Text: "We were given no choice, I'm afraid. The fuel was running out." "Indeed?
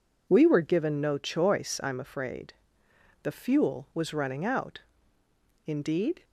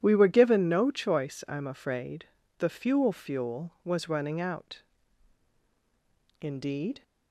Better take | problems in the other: first | says "fuel" twice; at 3.1 s

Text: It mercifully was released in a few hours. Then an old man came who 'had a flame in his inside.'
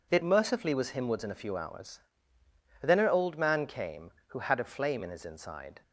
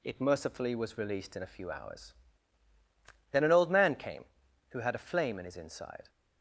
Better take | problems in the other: second | says "himwards" for "released"; at 0.9 s

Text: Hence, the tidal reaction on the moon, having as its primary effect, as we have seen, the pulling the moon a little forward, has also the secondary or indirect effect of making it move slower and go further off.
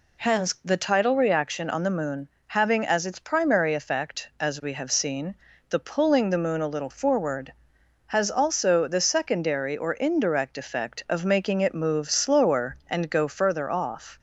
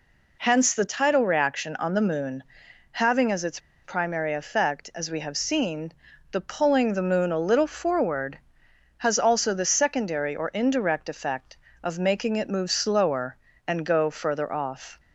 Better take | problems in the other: first | pauses between "its" and "primary"; slight; at 3.5 s; 0.26 s long

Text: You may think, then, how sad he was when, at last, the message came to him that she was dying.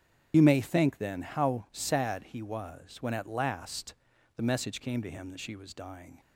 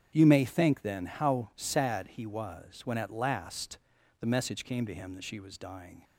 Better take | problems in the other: second | loses the start of "You"; at 0.3 s; 45 ms // starts louder than the rest; strong; until 1.3 s; 9 dB; strong in the second

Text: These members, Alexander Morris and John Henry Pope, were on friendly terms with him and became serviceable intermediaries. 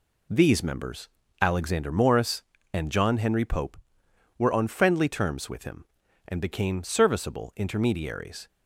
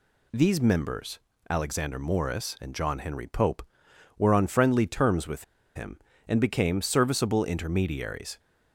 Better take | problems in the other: first | pauses between "with" and "him"; slight; at 5.4 s; 0.31 s long

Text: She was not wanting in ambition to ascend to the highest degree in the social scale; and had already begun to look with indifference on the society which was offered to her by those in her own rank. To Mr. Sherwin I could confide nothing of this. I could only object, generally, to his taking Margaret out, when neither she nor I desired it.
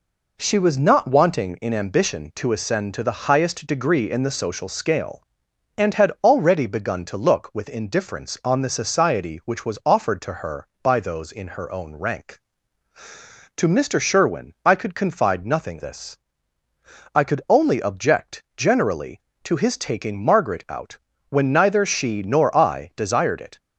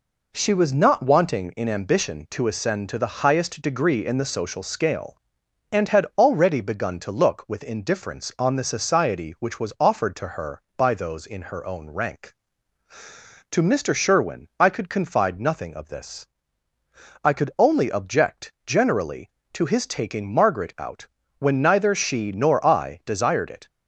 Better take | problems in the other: second | skips "of"; at 15.7 s

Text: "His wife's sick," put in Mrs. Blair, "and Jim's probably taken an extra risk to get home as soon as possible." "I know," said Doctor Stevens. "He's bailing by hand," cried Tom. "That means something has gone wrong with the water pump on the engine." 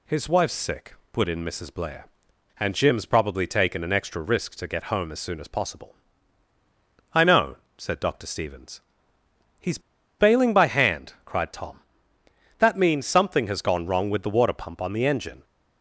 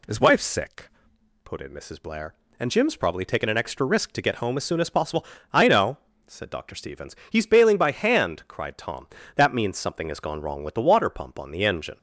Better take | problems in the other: second | pauses between "He's" and "bailing"; at 9.7 s; 0.40 s long

